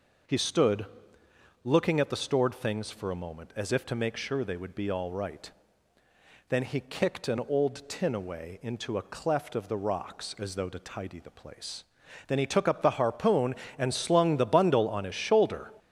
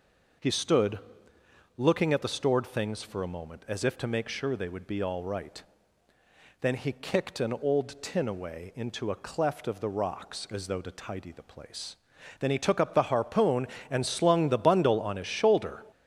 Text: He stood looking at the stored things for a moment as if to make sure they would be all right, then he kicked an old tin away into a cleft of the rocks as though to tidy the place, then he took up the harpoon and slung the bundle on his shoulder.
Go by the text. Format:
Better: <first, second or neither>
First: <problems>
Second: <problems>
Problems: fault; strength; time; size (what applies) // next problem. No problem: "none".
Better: neither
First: pauses between "stood" and "looking"; noticeable; at 0.8 s; 0.76 s long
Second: pauses between "stood" and "looking"; noticeable; at 0.9 s; 0.76 s long